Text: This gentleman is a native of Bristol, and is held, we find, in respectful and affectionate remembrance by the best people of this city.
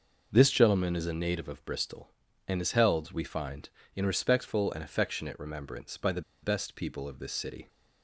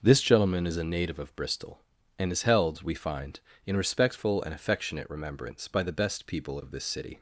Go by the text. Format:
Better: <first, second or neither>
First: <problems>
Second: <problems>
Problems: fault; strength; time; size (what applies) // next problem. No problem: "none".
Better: second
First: pauses between "the" and "best"; slight; at 6.2 s; 0.22 s long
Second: none